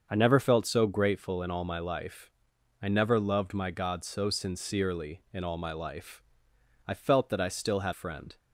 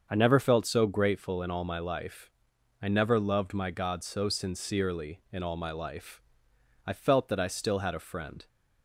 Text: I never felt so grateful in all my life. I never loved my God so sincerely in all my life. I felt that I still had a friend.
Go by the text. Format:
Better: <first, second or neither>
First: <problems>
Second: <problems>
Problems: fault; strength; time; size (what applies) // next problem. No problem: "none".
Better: second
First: starts louder than the rest; until 1.1 s; 6.5 dB // skips "a"; at 7.9 s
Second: starts louder than the rest; until 1.1 s; 6.5 dB